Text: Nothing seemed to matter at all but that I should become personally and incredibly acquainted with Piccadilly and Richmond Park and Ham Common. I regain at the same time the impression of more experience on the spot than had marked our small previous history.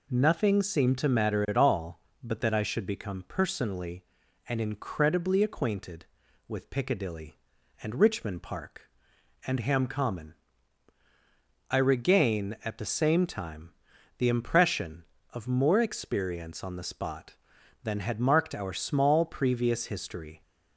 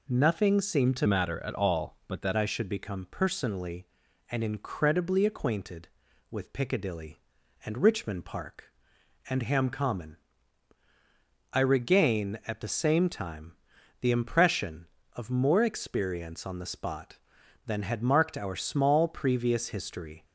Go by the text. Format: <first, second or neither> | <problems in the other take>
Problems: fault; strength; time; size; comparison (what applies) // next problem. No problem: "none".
first | changes voice from "matter" to "that"; from 1.0 to 2.3 s; 1.3 s long // pauses between "time" and "the"; noticeable; at 13.5 s; 0.48 s long; noticeable in the first